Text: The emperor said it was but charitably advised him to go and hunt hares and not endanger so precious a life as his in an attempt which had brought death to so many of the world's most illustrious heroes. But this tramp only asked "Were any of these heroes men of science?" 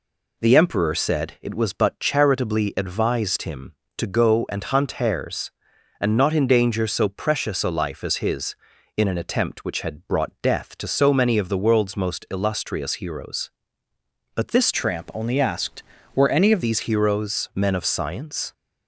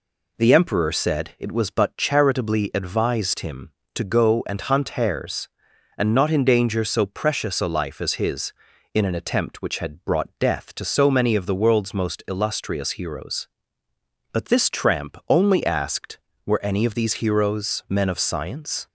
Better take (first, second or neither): second